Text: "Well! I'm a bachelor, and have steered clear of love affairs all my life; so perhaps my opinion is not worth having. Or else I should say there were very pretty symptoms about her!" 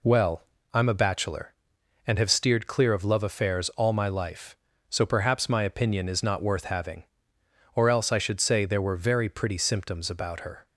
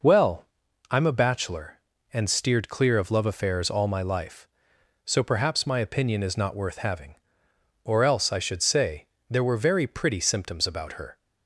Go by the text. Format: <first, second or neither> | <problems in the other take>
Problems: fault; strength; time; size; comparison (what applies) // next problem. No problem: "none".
first | skips "have"; at 2.2 s // pauses between "say" and "there"; slight; at 9.0 s; 0.20 s long